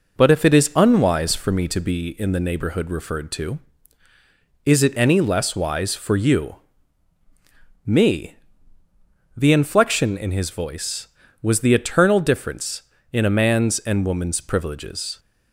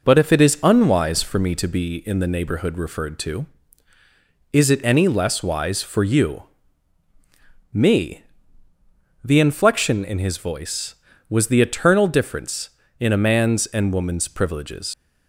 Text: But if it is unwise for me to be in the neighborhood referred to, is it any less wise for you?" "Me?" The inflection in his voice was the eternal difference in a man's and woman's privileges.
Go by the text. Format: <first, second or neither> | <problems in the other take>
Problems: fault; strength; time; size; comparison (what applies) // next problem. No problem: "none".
first | leaves "privileges" unfinished; at 14.9 s; 125 ms